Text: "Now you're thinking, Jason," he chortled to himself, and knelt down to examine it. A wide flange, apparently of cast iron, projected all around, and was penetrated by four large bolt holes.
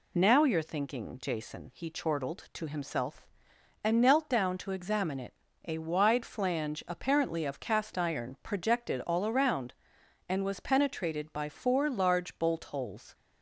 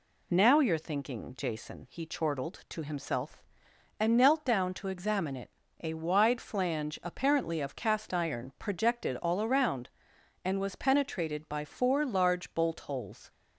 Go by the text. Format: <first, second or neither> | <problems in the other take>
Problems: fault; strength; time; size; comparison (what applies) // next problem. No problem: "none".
neither | none